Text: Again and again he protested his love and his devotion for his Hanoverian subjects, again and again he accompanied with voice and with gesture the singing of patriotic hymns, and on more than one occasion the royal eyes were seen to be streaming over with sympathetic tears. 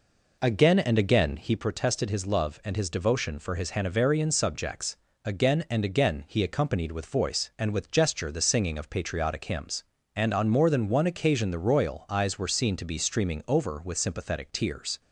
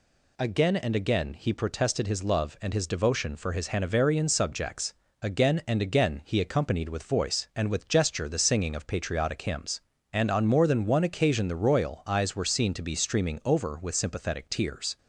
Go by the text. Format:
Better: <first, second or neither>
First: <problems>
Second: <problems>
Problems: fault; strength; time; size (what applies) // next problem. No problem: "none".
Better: second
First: starts louder than the rest; noticeable; until 1.5 s; 4 dB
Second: none